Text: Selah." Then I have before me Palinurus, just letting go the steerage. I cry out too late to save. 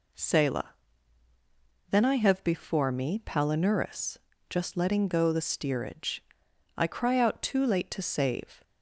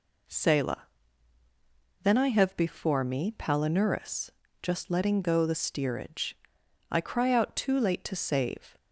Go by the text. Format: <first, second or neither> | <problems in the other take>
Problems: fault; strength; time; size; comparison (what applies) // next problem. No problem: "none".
neither | none